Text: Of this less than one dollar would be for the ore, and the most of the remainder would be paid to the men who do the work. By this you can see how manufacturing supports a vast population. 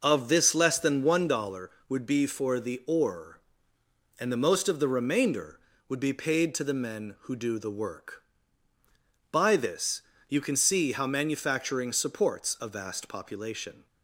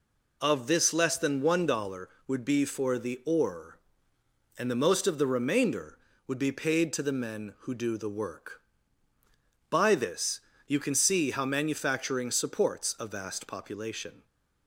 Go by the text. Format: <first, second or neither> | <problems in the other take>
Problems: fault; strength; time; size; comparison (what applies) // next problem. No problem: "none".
second | starts louder than the rest; noticeable; until 1.3 s; 5.5 dB // pauses between "this" and "you"; slight; at 10.0 s; 0.26 s long; slight in the second